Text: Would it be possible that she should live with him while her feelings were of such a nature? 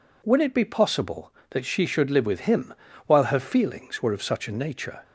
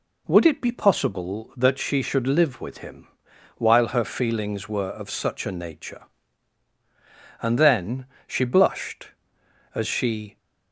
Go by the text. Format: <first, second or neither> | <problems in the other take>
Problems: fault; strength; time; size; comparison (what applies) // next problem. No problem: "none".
first | pauses between "him" and "while"; noticeable; at 3.0 s; 0.50 s long; slight in the first // goes on to say "And then she blushed as she"; strong; from 7.4 s on; 2.9 s long